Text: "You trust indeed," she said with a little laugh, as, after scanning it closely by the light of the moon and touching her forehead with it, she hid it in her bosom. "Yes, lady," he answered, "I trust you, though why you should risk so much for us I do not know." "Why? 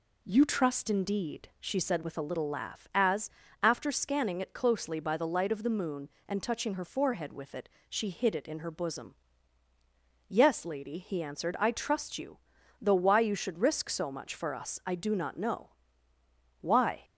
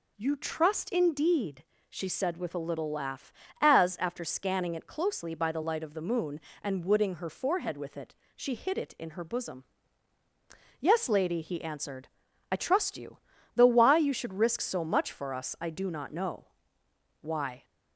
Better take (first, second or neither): first